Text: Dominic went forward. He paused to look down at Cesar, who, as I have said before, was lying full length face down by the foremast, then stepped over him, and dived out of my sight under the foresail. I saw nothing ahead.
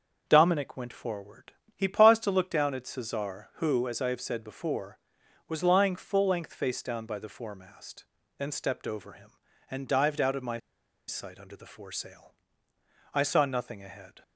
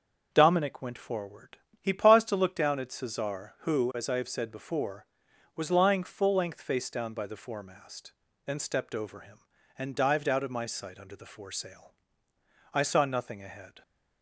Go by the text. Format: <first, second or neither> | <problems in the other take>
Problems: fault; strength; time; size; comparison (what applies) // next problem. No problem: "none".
second | starts louder than the rest; until 1.3 s; 6.5 dB; also in the second // pauses between "my" and "sight"; noticeable; at 10.5 s; 0.49 s long